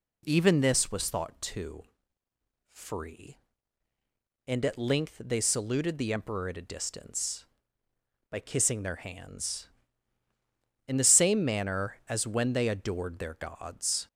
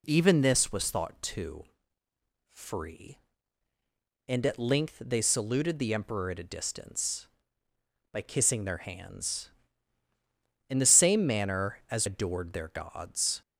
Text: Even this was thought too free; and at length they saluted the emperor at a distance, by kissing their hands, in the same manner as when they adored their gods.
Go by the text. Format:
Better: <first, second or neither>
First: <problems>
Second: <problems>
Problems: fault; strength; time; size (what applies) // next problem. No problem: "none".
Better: first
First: pauses between "too" and "free"; noticeable; at 1.8 s; 0.90 s long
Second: pauses between "too" and "free"; noticeable; at 1.6 s; 0.90 s long // skips "when they"; at 12.0 s